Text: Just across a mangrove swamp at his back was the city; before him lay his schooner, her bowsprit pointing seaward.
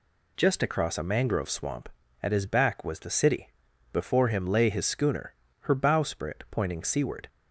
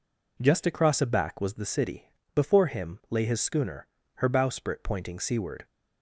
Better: first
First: none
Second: skips "mangrove swamp at his"; at 1.0 s

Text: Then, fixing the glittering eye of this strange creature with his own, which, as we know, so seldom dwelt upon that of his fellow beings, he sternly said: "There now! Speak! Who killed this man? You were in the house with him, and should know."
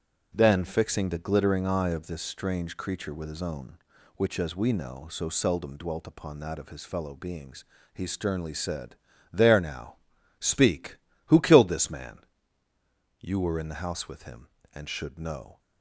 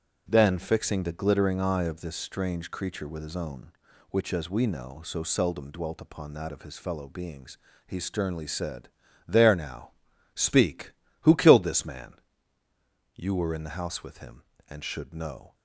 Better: neither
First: starts louder than the rest; strong; until 1.3 s; 7.5 dB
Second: starts louder than the rest; until 1.2 s; 6.5 dB

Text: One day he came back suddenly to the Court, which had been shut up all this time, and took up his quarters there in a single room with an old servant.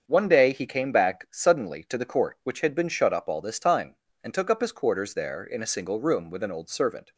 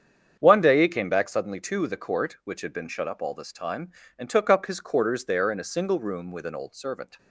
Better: neither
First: starts louder than the rest; until 1.0 s; 7 dB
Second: starts louder than the rest; strong; until 1.4 s; 8 dB

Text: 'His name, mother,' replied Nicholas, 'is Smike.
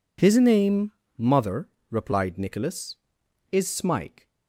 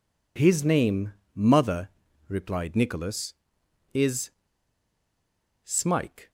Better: first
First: none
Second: pauses between "is" and "Smike"; strong; at 4.2 s; 1.3 s long

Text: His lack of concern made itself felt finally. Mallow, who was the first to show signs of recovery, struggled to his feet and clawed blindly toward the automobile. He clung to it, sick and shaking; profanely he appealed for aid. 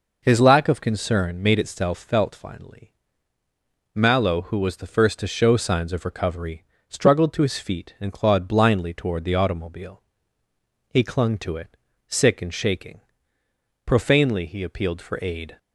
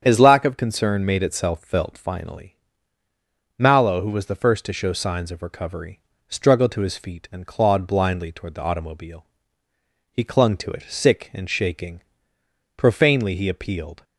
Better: first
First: none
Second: starts louder than the rest; strong; until 1.0 s; 8 dB // stops before "for aid"; at 14.0 s

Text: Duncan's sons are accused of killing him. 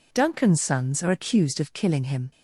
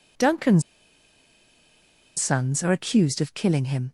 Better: first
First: none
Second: pauses between "Duncan's" and "sons"; strong; at 0.6 s; 1.5 s long

